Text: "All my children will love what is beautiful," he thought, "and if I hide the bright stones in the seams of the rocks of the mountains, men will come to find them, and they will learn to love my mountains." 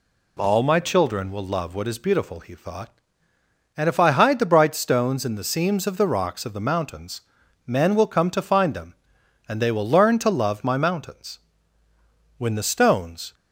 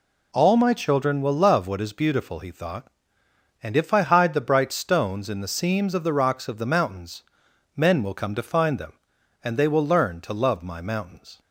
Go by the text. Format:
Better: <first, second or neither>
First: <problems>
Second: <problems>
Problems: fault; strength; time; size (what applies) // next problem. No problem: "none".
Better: second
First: goes on to say "When the stones"; noticeable; from 12.3 s on; 0.96 s long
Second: none